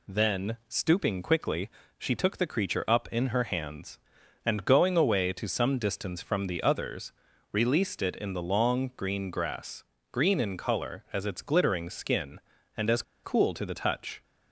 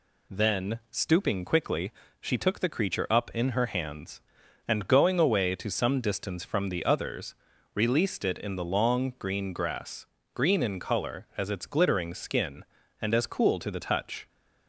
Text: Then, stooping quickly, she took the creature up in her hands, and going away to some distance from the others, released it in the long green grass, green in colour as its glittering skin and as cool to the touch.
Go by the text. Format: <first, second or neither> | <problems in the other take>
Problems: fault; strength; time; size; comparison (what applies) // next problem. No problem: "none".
second | pauses between "as" and "cool"; slight; at 13.0 s; 0.21 s long